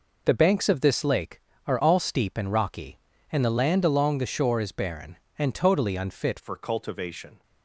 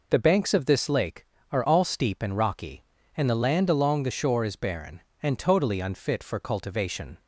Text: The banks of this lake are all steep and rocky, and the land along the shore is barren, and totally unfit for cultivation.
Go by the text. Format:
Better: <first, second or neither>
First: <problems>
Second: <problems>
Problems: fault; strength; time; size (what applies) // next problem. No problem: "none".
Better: second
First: changes voice at "for"; from 6.4 s on; 1.0 s long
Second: none